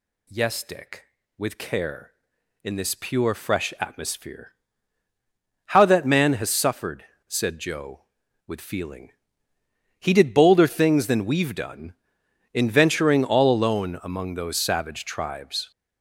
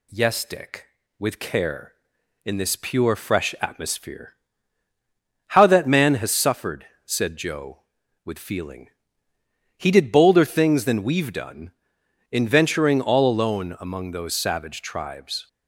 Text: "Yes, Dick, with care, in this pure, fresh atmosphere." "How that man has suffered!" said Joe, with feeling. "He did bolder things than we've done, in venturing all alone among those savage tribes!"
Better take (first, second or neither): second